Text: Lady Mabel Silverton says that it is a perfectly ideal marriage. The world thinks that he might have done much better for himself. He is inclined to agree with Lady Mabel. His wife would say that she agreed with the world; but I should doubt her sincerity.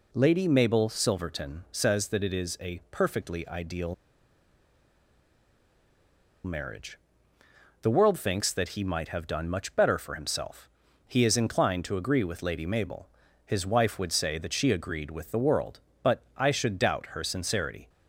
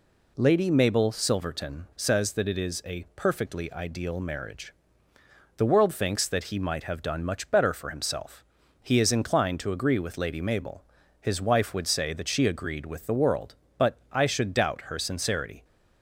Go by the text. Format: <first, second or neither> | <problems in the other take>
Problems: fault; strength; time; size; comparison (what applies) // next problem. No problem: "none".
second | pauses between "ideal" and "marriage"; strong; at 3.9 s; 2.5 s long // pauses between "but" and "I"; slight; at 16.2 s; 0.16 s long; slight in the second